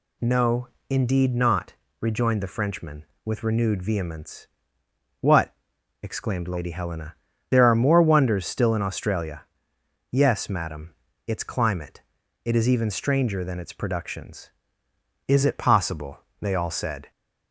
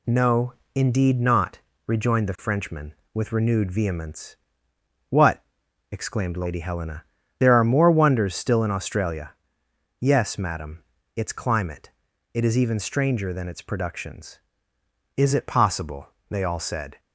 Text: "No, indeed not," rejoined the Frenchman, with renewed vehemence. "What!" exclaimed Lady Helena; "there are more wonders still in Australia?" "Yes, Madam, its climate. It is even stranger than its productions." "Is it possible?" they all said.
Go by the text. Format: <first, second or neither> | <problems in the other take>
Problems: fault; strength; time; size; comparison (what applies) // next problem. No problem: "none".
first | gets quieter; noticeable; throughout; 4 dB